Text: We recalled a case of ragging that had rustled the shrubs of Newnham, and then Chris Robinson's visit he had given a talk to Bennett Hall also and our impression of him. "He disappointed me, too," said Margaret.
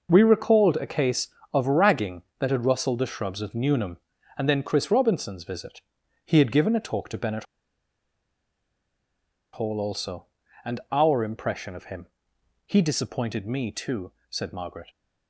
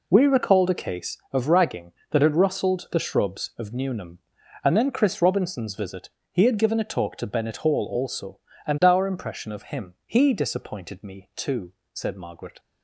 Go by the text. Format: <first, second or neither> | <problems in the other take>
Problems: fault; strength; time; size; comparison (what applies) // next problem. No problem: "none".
second | pauses between "visit" and "he"; at 5.8 s; 0.44 s long; slight in the second // pauses between "Bennett" and "Hall"; strong; at 7.4 s; 2.0 s long